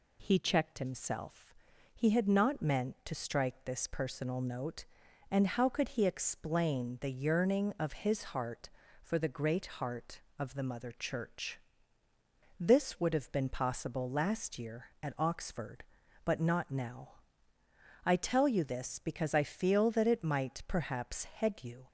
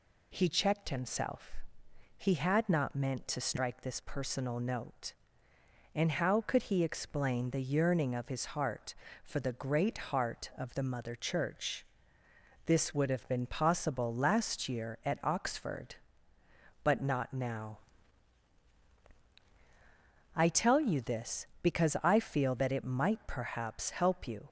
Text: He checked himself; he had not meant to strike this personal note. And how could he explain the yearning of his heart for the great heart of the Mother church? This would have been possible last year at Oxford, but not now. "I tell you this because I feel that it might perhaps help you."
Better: second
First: pauses between "great" and "heart"; slight; at 9.6 s; 0.16 s long // says "head" for "help"; at 21.2 s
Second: none

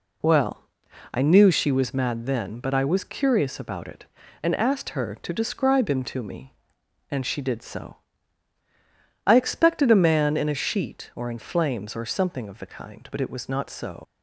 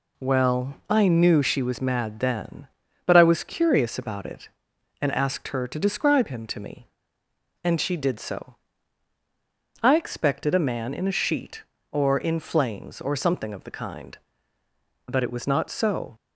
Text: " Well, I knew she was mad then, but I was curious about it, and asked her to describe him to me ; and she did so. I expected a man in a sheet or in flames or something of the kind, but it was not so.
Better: second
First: leaves "so" unfinished; at 14.0 s; 85 ms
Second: none

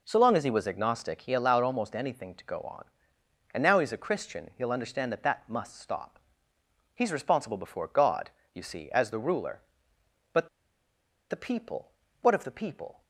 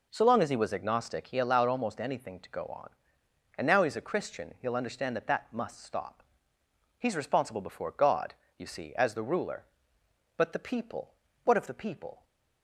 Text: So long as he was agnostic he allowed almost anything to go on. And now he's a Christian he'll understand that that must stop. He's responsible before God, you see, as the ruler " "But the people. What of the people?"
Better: second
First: pauses between "But" and "the"; noticeable; at 10.4 s; 0.82 s long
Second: none

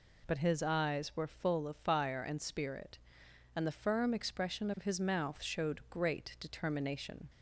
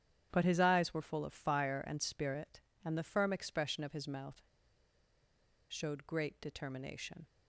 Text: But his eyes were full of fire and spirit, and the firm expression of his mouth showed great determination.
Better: first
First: none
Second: starts louder than the rest; strong; until 1.3 s; 9 dB // pauses between "mouth" and "showed"; strong; at 4.4 s; 1.2 s long

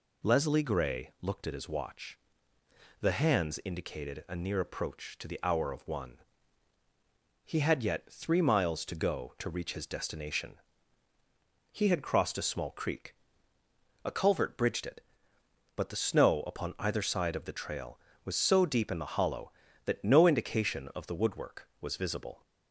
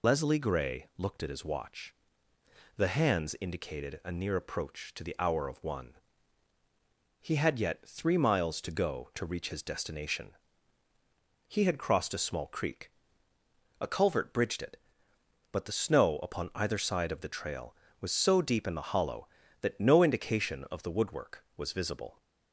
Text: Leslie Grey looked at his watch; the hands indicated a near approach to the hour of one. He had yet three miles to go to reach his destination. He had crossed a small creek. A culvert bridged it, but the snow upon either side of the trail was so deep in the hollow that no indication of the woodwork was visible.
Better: first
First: none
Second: loses the start of "Leslie"; at 0.0 s; 45 ms

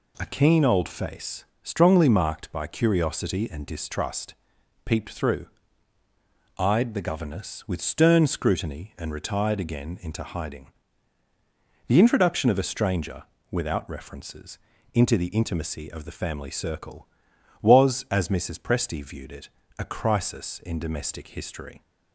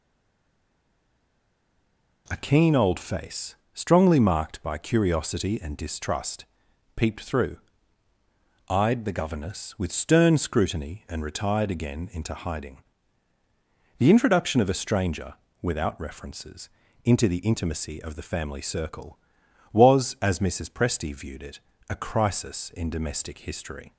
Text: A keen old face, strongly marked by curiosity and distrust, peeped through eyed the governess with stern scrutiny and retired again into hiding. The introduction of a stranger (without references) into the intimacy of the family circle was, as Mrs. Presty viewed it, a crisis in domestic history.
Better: first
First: pauses between "through" and "eyed"; at 5.4 s; 1.1 s long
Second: stays silent before the first word; until 2.2 s; 2.2 s long // pauses between "through" and "eyed"; at 7.5 s; 1.1 s long

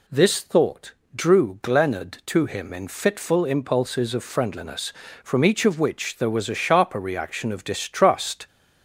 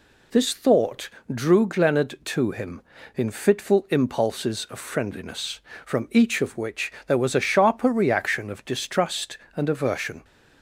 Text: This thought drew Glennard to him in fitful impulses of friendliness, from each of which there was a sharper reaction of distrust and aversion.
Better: second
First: pauses between "thought" and "drew"; slight; at 0.9 s; 0.24 s long // stops before "and aversion"; at 8.4 s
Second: pauses between "thought" and "drew"; slight; at 1.0 s; 0.26 s long

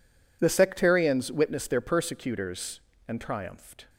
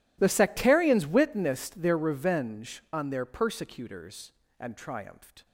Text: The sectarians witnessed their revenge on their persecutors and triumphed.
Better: second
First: skips "their revenge on"; at 1.6 s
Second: none

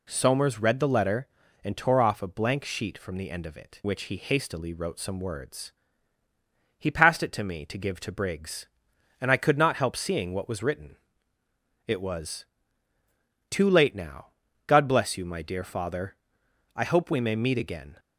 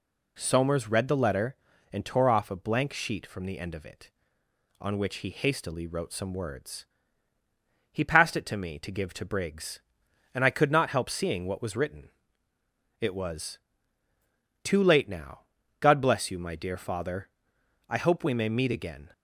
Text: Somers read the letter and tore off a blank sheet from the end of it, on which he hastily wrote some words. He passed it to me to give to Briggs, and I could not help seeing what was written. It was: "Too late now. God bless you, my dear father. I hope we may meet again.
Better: second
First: skips "on"; at 3.8 s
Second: none

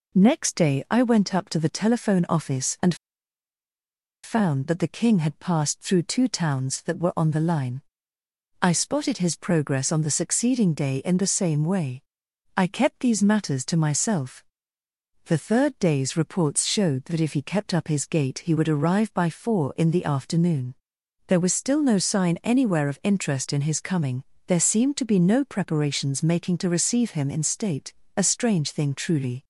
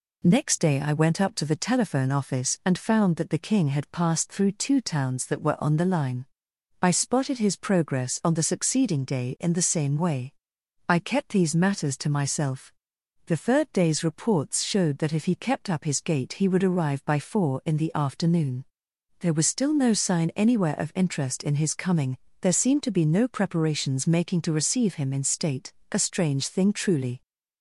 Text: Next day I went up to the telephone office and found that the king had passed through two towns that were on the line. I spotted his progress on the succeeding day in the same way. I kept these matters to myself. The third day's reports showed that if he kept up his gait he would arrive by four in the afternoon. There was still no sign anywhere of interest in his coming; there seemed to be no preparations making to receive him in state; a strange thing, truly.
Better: second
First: pauses between "and" and "found"; strong; at 2.9 s; 1.2 s long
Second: none

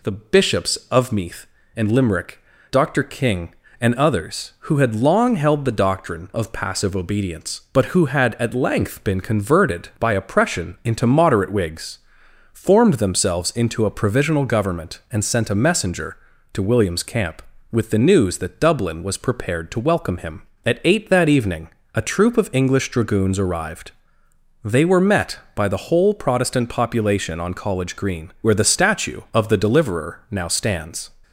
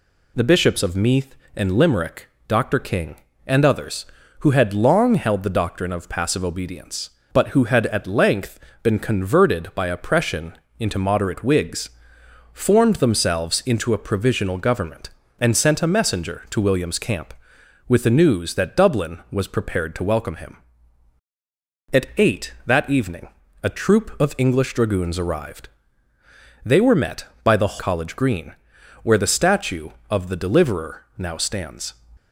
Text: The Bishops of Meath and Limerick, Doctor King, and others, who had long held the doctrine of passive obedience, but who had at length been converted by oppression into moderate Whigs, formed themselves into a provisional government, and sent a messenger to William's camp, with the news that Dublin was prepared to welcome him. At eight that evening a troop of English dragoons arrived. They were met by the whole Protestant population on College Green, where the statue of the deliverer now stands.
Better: first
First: pauses between "evening" and "a"; slight; at 21.6 s; 0.24 s long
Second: pauses between "length" and "been"; slight; at 8.5 s; 0.24 s long // pauses between "oppression" and "into"; slight; at 10.5 s; 0.20 s long // pauses between "evening" and "a"; slight; at 23.2 s; 0.34 s long // skips "whole Protestant population on"; at 27.7 s

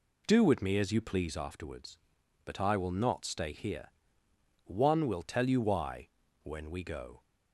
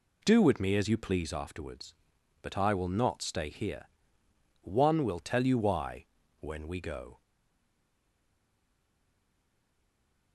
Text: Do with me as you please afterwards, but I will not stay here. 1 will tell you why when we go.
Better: first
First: pauses between "why" and "when"; slight; at 6.0 s; 0.36 s long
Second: pauses between "why" and "when"; slight; at 6.0 s; 0.36 s long // stays silent after the last word; strong; from 7.2 s on; 3.1 s long

